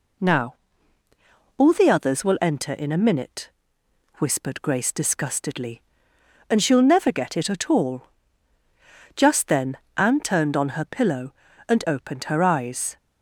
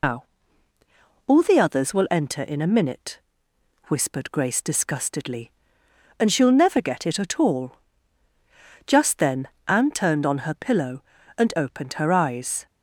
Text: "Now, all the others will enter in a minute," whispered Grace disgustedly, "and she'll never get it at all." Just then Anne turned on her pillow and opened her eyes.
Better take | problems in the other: first | loses the start of "Now"; at 0.0 s; 140 ms // pauses between "then" and "Anne"; slight; at 9.4 s; 0.20 s long; slight in the first

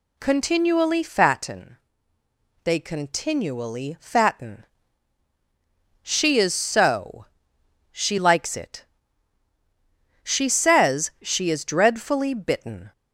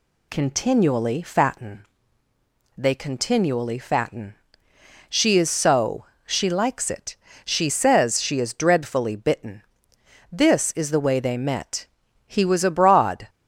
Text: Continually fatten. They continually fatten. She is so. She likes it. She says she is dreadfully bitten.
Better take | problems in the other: first | goes on to say "This is the way they met He was abroad"; strong; from 10.3 s on; 2.9 s long

